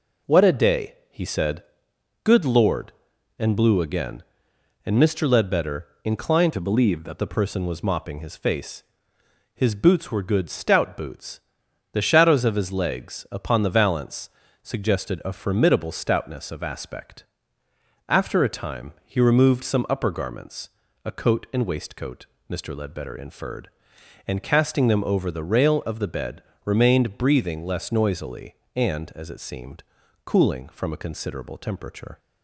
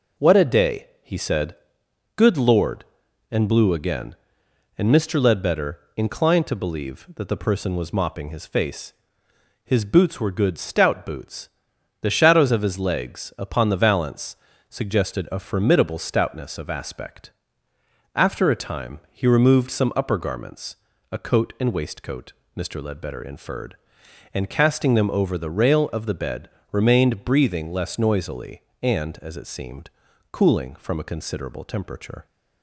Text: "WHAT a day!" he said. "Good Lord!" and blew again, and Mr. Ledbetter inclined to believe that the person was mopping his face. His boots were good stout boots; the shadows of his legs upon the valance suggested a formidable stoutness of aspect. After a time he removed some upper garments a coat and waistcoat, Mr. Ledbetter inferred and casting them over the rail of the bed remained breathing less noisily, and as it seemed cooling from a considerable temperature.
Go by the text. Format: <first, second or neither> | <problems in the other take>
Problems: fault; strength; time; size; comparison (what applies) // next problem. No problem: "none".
second | pauses between "Ledbetter" and "inclined"; slight; at 5.8 s; 0.16 s long; slight in the second // changes voice from "to" to "that"; from 6.5 to 7.1 s; 0.6 s long // pauses between "valance" and "suggested"; slight; at 14.2 s; 0.34 s long; slight in the second // pauses between "garments" and "a"; slight; at 20.6 s; 0.36 s long; slight in the second // pauses between "bed" and "remained"; slight; at 26.4 s; 0.20 s long; slight in the second // pauses between "seemed" and "cooling"; at 29.8 s; 0.42 s long; also in the second